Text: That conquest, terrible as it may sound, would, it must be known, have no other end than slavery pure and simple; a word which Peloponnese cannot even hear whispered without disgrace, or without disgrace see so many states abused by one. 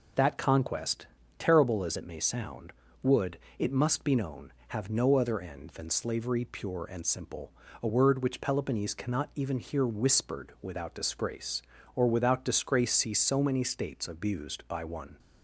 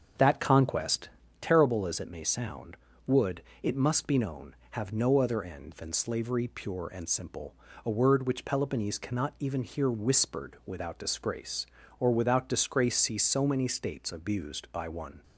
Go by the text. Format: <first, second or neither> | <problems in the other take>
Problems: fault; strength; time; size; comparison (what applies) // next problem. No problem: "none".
first | starts louder than the rest; until 1.3 s; 7 dB